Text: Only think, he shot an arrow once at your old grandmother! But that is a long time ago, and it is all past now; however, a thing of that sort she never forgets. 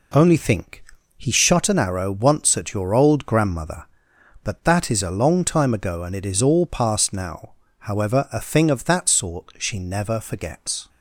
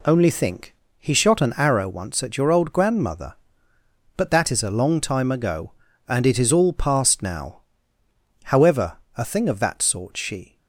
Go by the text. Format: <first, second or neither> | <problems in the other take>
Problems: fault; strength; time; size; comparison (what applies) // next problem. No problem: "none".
first | stops before "never forgets"; at 10.5 s